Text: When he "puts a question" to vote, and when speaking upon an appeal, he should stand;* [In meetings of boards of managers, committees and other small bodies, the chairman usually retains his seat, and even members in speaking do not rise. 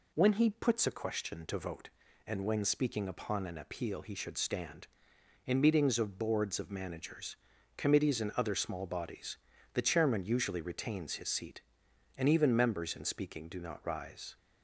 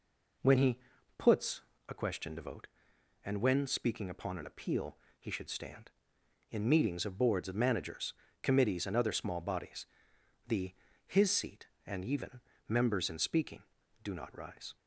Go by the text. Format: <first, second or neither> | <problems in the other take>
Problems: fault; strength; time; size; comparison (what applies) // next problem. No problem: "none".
first | pauses between "he" and "puts"; at 0.7 s; 0.38 s long // pauses between "puts" and "a"; slight; at 1.6 s; 0.26 s long // skips "chairman usually retains"; at 10.9 s // pauses between "even" and "members"; slight; at 12.3 s; 0.28 s long